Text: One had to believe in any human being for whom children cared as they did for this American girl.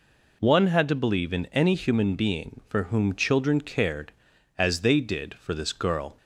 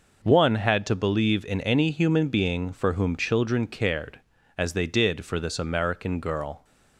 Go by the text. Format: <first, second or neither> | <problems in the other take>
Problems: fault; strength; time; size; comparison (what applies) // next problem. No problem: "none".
second | skips "American"; at 5.7 s